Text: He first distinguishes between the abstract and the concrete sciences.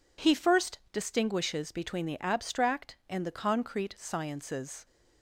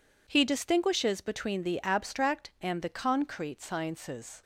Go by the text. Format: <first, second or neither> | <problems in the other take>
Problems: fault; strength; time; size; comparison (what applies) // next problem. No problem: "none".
first | skips "first"; at 0.4 s